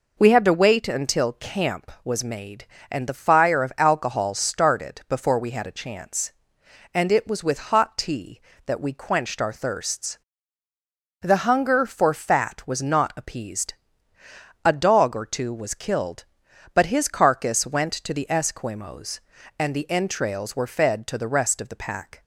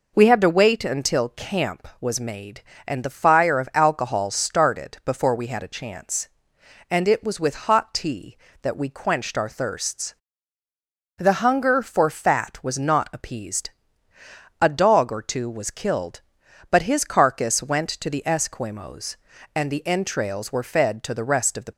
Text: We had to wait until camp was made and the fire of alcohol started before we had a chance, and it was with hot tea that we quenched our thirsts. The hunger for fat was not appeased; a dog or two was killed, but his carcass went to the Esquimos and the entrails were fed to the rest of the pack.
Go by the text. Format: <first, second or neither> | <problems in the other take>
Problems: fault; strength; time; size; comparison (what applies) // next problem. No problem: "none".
first | stops before "pack"; at 21.7 s